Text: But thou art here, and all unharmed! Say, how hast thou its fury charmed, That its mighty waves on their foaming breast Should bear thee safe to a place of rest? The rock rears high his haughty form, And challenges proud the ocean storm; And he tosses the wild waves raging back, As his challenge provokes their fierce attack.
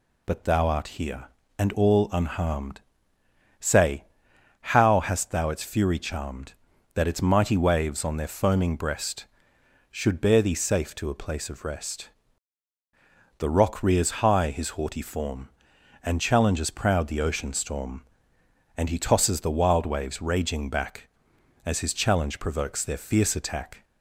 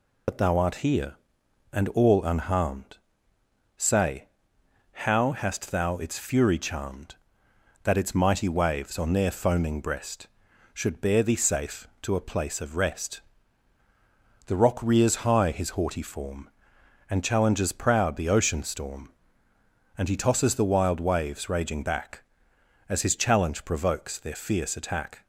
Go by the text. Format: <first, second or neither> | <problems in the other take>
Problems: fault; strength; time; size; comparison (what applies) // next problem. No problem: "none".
first | loses the start of "But"; at 0.2 s; 50 ms